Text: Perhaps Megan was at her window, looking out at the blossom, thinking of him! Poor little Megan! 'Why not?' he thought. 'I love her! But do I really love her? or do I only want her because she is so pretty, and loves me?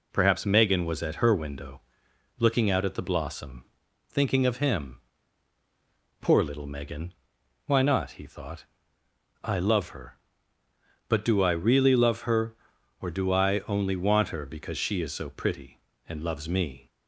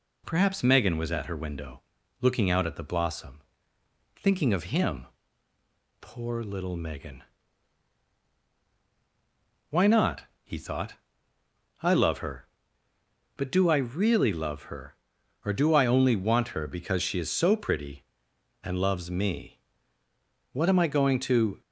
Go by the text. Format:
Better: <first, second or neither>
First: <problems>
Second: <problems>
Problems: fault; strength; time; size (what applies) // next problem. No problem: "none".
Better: first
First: none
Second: goes on to say "What am I going to"; noticeable; from 20.5 s on; 1.0 s long